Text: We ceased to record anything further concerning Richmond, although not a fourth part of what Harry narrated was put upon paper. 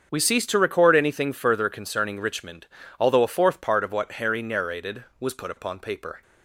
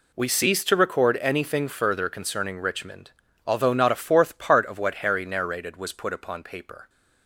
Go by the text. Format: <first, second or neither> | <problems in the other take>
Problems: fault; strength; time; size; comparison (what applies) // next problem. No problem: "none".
second | starts louder than the rest; strong; until 1.1 s; 7.5 dB // skips "not"; at 3.2 s